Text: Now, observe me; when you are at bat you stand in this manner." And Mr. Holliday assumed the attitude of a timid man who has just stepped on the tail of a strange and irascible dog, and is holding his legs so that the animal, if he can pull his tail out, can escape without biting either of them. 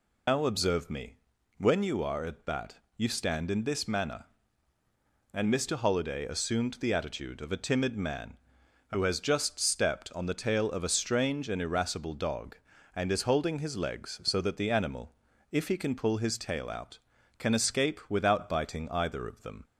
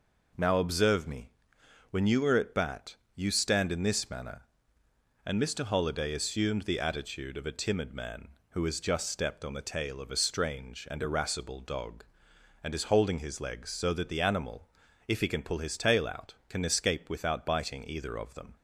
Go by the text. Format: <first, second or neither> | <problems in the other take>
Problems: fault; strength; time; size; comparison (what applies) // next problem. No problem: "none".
second | loses the start of "Now"; at 0.2 s; 145 ms // pauses between "bat" and "you"; slight; at 2.7 s; 0.18 s long; slight in the second